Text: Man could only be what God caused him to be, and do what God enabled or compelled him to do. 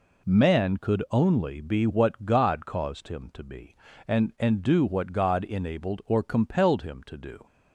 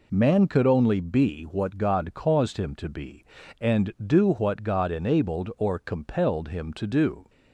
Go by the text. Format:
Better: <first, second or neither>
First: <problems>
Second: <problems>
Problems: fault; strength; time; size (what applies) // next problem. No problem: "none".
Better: second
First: says "and" twice; at 4.3 s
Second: none